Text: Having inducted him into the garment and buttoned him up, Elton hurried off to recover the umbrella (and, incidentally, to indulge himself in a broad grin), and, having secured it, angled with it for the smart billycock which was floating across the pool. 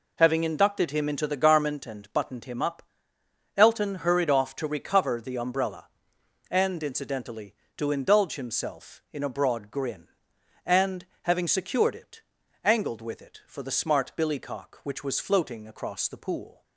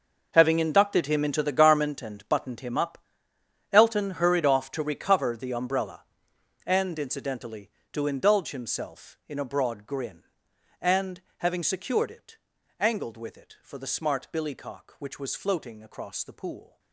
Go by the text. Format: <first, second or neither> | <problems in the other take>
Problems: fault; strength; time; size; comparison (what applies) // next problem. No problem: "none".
first | gets quieter; strong; throughout; 14.5 dB